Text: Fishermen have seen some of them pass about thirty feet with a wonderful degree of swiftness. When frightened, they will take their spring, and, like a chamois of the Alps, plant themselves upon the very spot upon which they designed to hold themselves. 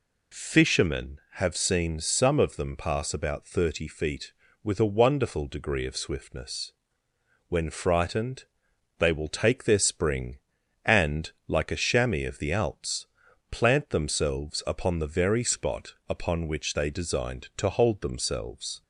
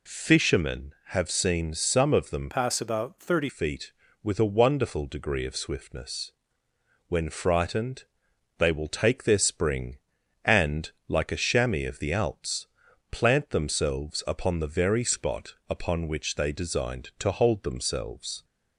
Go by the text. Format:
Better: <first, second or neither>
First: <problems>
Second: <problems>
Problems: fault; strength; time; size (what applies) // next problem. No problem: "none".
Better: first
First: pauses between "spot" and "upon"; slight; at 15.9 s; 0.16 s long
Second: changes voice from "pass" to "thirty"; from 2.5 to 3.4 s; 0.9 s long // pauses between "spot" and "upon"; slight; at 15.5 s; 0.16 s long